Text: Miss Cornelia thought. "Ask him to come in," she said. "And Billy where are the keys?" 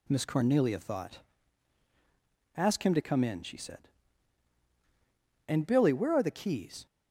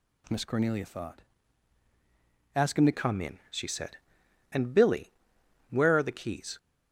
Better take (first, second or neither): first